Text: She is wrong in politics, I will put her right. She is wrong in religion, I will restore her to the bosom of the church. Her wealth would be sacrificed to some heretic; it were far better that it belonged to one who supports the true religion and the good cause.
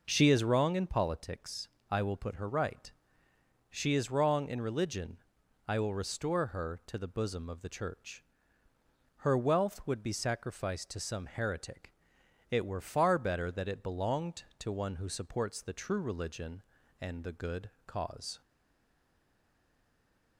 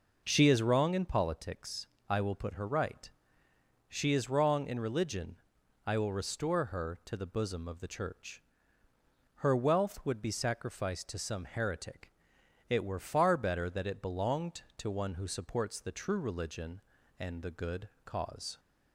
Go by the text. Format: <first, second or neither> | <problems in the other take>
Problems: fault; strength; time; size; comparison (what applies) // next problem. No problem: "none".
second | pauses between "good" and "cause"; slight; at 17.7 s; 0.16 s long; slight in the second // stays silent after the last word; noticeable; from 18.4 s on; 1.9 s long